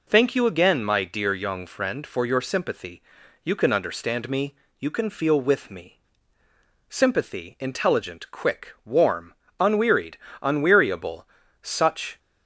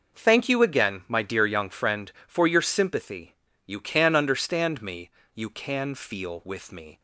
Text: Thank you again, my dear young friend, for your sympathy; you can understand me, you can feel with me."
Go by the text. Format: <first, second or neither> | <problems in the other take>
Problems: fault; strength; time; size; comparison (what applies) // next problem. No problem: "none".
second | goes on to say "Sympathy intelligent quick warm unwearied unweariable such"; strong; from 6.9 s on; 5.2 s long